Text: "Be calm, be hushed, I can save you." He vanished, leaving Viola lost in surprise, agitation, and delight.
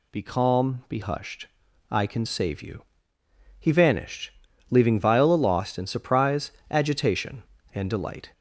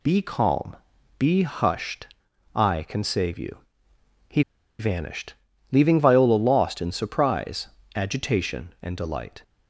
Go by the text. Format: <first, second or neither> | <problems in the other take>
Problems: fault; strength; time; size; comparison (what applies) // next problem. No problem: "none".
first | pauses between "He" and "vanished"; at 4.4 s; 0.38 s long